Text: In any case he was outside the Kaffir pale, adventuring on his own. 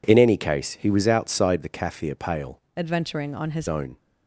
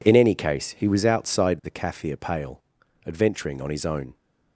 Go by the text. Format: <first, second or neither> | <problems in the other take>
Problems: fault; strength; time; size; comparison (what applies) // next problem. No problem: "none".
second | changes voice from "adventuring" to "his"; from 2.7 to 3.6 s; 0.9 s long